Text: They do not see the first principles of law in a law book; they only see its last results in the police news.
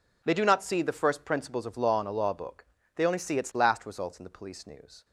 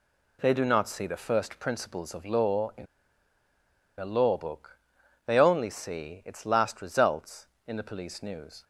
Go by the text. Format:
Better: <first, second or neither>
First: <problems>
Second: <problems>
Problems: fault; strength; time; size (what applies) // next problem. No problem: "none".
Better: first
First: none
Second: pauses between "in" and "a"; at 2.8 s; 1.1 s long